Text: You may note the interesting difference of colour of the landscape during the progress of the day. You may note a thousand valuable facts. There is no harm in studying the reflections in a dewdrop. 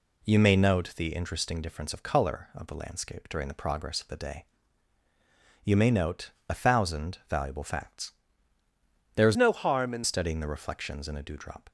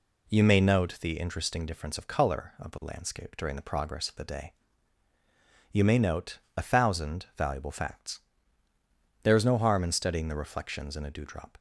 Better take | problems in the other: second | pauses between "note" and "a"; slight; at 6.3 s; 0.18 s long; slight in the second // changes voice from "no" to "in"; from 9.3 to 10.0 s; 0.7 s long

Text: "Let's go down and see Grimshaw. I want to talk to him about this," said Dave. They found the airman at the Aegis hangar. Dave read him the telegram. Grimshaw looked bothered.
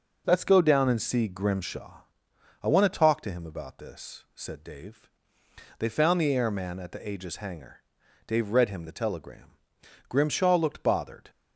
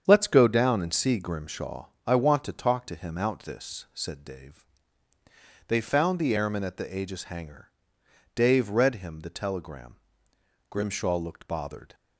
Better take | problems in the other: first | starts louder than the rest; strong; until 1.0 s; 8 dB // says "out" for "about"; at 3.1 s

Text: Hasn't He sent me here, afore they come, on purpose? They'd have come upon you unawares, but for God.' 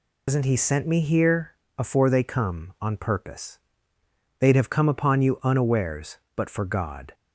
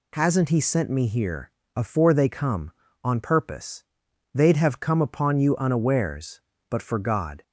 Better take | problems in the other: second | loses the start of "Hasn't"; at 0.2 s; 130 ms

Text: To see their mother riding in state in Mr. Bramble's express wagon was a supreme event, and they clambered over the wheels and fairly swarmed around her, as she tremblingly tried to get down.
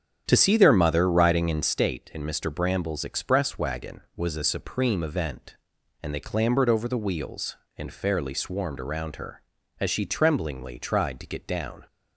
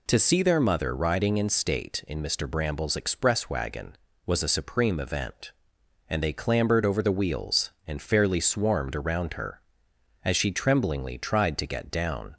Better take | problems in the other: second | starts louder than the rest; strong; until 1.7 s; 8 dB

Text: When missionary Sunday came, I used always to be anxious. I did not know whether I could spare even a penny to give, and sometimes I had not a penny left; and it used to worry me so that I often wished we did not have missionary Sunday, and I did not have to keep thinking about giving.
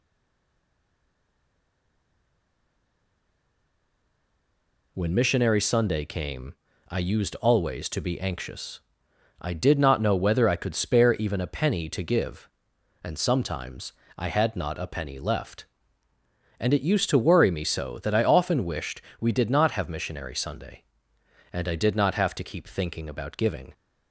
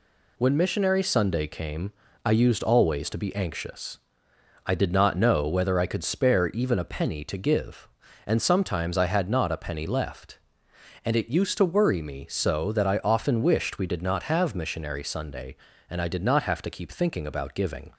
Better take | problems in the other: second | stays silent before the first word; strong; until 4.9 s; 4.9 s long // pauses between "sometimes" and "I"; slight; at 13.9 s; 0.24 s long // pauses between "wished" and "we"; slight; at 18.9 s; 0.18 s long

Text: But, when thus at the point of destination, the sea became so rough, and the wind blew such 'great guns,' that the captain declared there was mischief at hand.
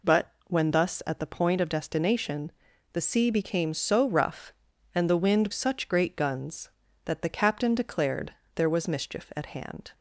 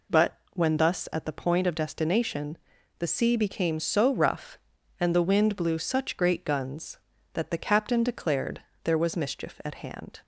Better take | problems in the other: second | skips "blew"; at 5.5 s // pauses between "declared" and "there"; slight; at 8.3 s; 0.22 s long; slight in the second

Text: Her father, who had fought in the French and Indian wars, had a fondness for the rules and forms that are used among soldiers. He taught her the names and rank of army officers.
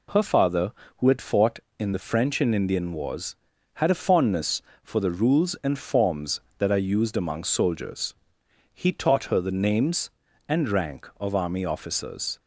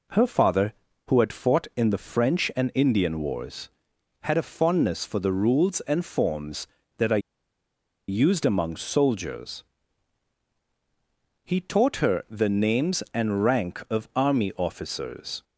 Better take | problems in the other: first | pauses between "are" and "used"; noticeable; at 7.2 s; 0.90 s long

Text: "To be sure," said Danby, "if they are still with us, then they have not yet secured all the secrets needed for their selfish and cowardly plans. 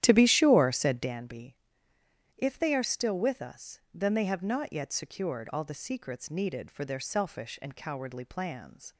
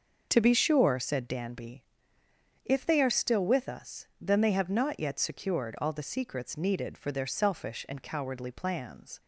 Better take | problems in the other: second | starts louder than the rest; strong; until 1.2 s; 11.5 dB

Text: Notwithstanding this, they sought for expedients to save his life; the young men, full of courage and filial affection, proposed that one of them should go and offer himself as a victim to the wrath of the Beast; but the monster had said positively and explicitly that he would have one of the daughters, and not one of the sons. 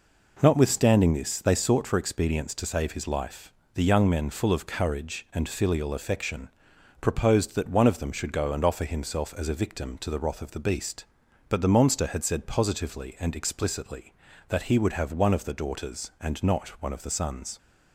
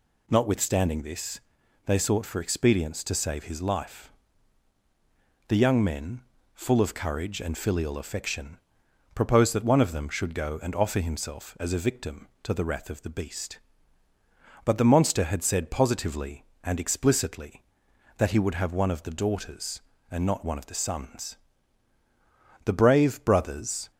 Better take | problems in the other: first | goes on to say "The brave brothers"; noticeable; from 22.6 s on; 1.2 s long

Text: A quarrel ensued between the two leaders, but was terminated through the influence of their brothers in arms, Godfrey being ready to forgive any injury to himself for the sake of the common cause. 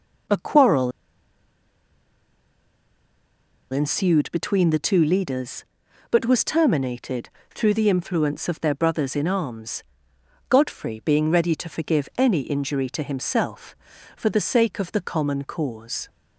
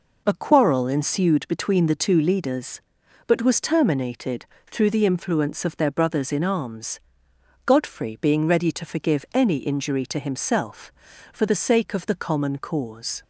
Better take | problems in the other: second | pauses between "quarrel" and "ensued"; strong; at 0.9 s; 2.7 s long // pauses between "terminated" and "through"; slight; at 7.2 s; 0.26 s long; slight in the second

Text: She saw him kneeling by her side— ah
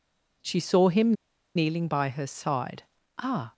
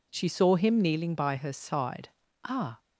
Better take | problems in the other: second | pauses between "him" and "kneeling"; at 1.1 s; 0.42 s long

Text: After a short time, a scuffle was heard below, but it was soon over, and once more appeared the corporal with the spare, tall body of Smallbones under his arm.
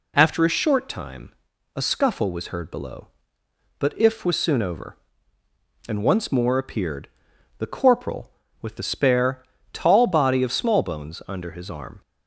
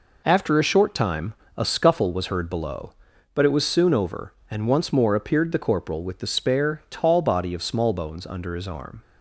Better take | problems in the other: second | says "if" for "it"; at 3.9 s // pauses between "appeared" and "the"; noticeable; at 7.0 s; 0.50 s long

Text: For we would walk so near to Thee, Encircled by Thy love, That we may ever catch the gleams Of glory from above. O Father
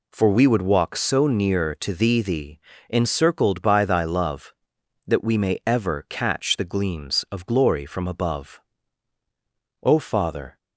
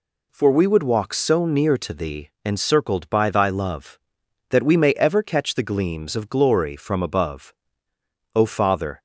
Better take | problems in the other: second | says "Thee" twice; at 2.2 s

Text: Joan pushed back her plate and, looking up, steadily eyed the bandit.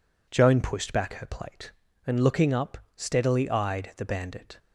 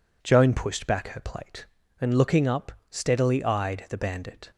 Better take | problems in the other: neither | none

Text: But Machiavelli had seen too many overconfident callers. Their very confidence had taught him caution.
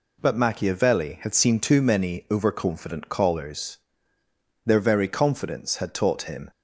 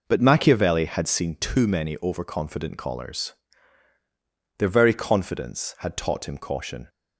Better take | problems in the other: second | stops before "caution"; at 6.5 s

